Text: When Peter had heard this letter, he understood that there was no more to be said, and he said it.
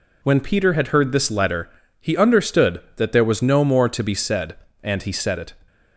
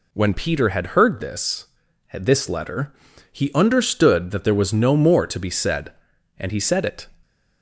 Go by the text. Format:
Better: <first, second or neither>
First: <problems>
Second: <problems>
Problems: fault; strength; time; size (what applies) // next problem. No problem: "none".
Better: first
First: none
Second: says "this" twice; at 2.1 s